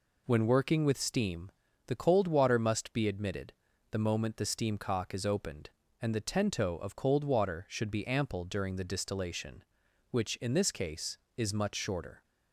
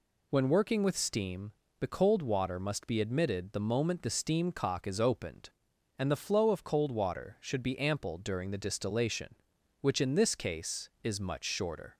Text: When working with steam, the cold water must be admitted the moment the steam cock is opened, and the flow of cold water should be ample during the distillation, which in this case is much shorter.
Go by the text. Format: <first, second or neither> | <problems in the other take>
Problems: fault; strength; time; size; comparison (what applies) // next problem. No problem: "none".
second | pauses between "admitted" and "the"; at 3.5 s; 0.40 s long // says "tento" for "flow"; at 6.2 s